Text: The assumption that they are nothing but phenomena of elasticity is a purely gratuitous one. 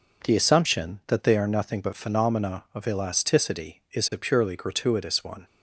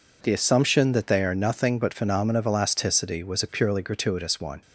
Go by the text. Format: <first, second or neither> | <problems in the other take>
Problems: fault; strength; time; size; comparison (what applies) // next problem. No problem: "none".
first | says "was" for "is"; at 3.2 s